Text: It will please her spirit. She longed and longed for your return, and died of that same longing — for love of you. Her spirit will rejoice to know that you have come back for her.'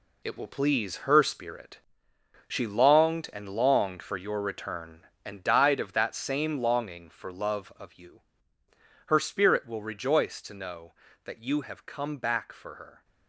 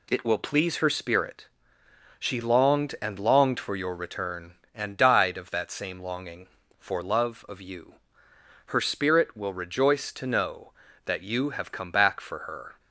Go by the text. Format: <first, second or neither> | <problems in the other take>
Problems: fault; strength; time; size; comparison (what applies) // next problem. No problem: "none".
second | gets quieter; strong; throughout; 9 dB